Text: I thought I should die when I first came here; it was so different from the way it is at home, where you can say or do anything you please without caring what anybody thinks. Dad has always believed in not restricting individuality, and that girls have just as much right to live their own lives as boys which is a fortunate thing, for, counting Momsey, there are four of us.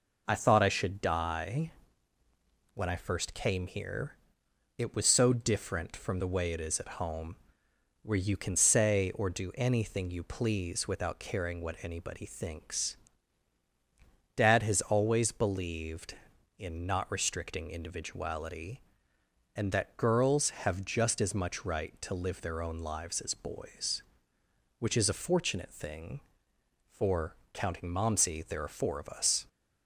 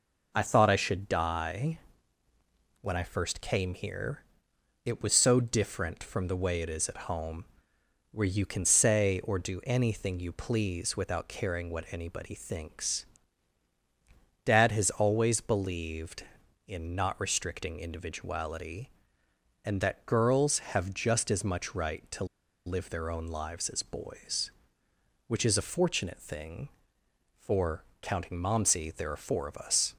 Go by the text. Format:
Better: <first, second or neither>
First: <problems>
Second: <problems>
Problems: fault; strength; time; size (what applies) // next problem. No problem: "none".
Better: first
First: pauses between "die" and "when"; at 1.7 s; 1.0 s long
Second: pauses between "die" and "when"; at 1.7 s; 1.0 s long // pauses between "to" and "live"; at 22.2 s; 0.41 s long